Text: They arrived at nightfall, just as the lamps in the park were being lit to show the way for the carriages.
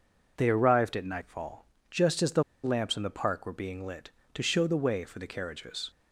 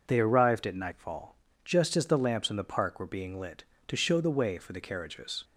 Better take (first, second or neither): second